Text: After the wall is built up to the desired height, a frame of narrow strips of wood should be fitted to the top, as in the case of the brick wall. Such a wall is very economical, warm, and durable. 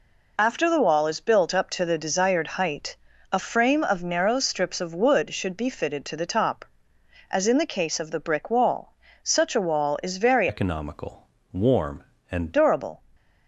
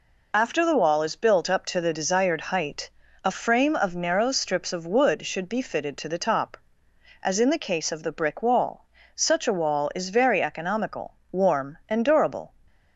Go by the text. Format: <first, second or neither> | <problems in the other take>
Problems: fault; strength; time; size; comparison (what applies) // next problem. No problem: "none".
second | changes voice from "economical" to "and"; from 10.4 to 12.5 s; 2.1 s long